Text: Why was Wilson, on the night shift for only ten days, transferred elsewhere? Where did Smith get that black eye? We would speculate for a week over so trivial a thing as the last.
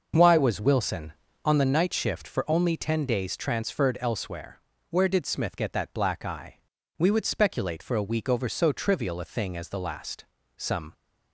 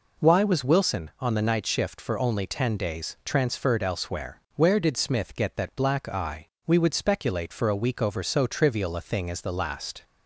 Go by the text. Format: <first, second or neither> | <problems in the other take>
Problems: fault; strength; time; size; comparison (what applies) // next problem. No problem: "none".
second | starts louder than the rest; noticeable; until 1.4 s; 6 dB // goes on to say "Some"; slight; from 10.5 s on; 0.38 s long